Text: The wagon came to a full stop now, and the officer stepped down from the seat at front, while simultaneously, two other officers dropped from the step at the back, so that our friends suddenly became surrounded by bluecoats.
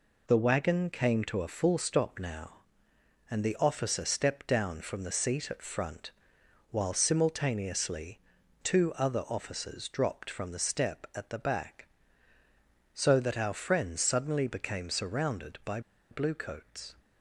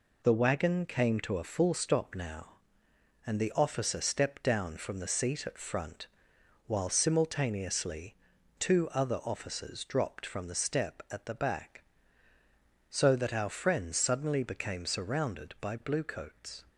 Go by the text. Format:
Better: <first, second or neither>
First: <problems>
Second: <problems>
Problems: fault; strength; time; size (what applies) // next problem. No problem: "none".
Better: second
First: pauses between "by" and "bluecoats"; slight; at 15.7 s; 0.31 s long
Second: none